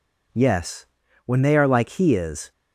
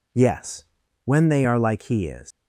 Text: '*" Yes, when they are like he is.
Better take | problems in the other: first | leaves "is" unfinished; at 2.3 s; 110 ms

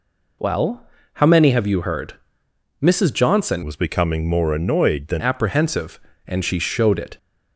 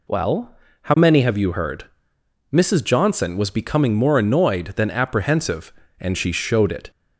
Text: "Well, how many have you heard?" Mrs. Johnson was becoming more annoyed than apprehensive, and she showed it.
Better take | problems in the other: second | changes voice from "was" to "than"; from 3.6 to 5.2 s; 1.6 s long

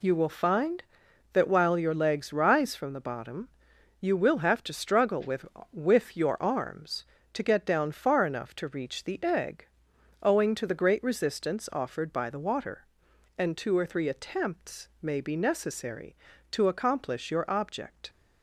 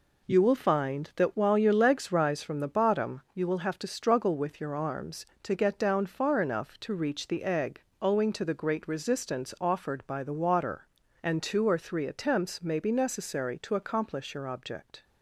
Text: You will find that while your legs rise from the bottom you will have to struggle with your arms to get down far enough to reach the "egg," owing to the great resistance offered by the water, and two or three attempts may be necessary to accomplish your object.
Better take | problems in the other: second | pauses between "bottom" and "you"; noticeable; at 3.4 s; 0.52 s long // says "with" twice; at 5.7 s // pauses between "attempts" and "may"; slight; at 14.8 s; 0.16 s long

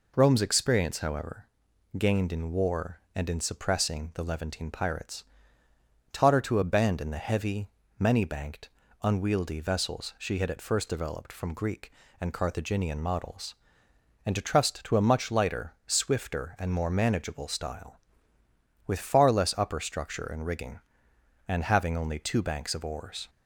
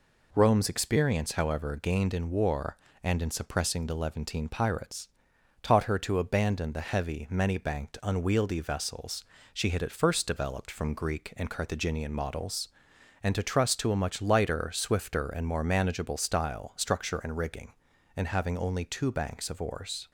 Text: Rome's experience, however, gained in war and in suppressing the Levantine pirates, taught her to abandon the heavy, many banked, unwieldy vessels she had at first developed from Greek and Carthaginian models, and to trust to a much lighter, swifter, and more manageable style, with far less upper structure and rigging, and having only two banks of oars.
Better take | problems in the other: first | pauses between "vessels" and "she"; slight; at 9.2 s; 0.28 s long // skips "with far less upper"; at 16.7 s

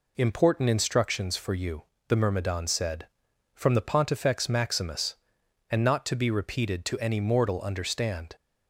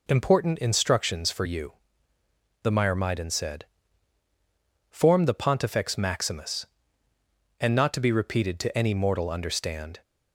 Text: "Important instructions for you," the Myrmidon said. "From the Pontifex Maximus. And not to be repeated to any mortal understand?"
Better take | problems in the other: first | says "Form" for "From"; at 4.9 s

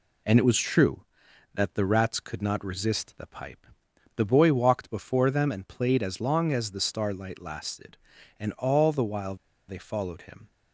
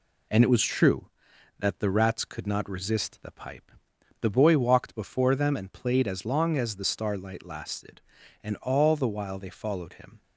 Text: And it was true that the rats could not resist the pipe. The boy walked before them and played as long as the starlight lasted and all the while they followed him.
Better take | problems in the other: second | pauses between "while" and "they"; slight; at 9.3 s; 0.34 s long

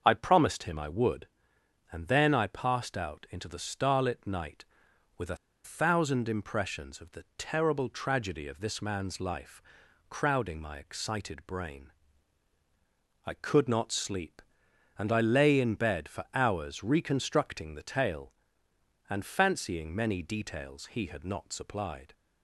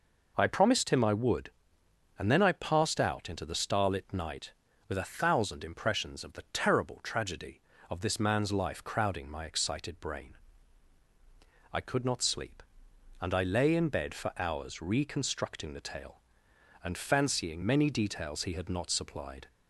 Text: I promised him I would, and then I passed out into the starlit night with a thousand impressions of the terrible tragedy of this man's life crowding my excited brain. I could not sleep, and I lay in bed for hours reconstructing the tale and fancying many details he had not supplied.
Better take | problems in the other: second | starts louder than the rest; until 1.0 s; 6.5 dB // pauses between "a" and "thousand"; slight; at 5.3 s; 0.27 s long // pauses between "life" and "crowding"; noticeable; at 9.6 s; 0.48 s long

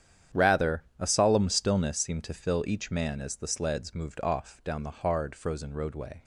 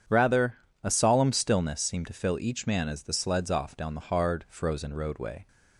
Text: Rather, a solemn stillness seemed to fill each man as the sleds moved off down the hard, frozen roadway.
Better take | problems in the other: first | starts louder than the rest; strong; until 1.3 s; 8.5 dB; strong in the first // skips "moved"; at 3.5 s

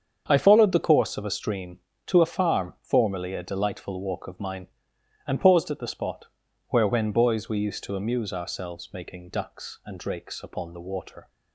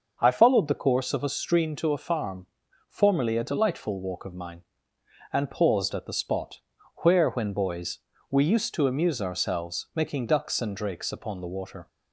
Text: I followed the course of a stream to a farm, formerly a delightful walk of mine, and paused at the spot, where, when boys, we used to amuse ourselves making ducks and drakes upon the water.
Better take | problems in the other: neither | starts louder than the rest; the same in both

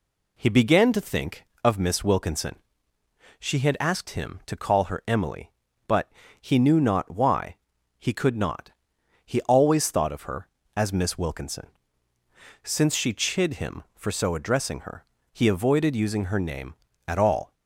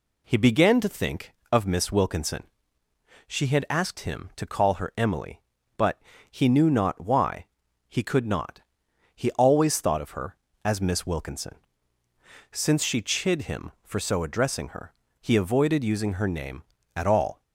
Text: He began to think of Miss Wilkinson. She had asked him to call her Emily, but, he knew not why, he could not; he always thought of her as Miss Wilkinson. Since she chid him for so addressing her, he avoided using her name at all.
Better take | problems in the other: neither | none

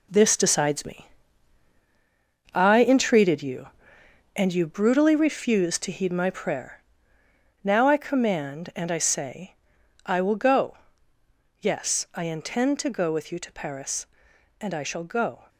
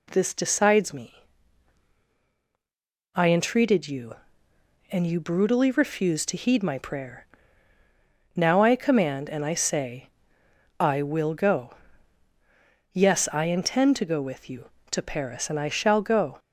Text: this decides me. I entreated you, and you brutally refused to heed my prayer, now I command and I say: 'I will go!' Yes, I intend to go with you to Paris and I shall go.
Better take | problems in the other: second | gets quieter; strong; throughout; 8.5 dB

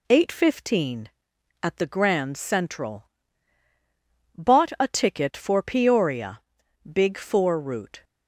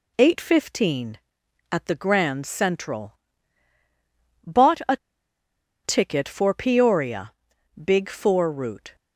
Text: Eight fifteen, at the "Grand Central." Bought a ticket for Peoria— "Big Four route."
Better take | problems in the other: first | pauses between "a" and "ticket"; noticeable; at 4.9 s; 0.88 s long

